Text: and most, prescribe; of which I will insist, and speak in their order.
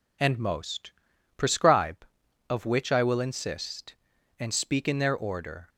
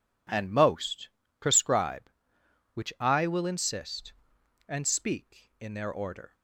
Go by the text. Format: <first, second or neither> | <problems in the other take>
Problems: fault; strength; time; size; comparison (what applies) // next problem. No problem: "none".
first | skips "of"; at 2.4 s